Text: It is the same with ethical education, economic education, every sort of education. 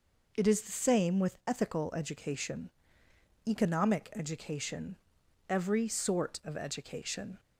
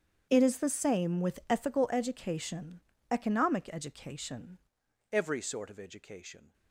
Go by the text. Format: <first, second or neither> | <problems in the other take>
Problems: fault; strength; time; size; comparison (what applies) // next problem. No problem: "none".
first | starts louder than the rest; strong; until 1.3 s; 8 dB // changes voice at "every"; from 5.1 s on; 1.4 s long